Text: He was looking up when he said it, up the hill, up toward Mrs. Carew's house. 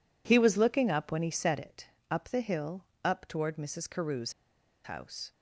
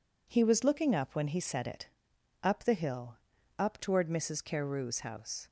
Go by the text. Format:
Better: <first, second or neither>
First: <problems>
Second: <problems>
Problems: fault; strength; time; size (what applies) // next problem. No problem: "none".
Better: second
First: pauses between "Carew's" and "house"; noticeable; at 4.3 s; 0.52 s long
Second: none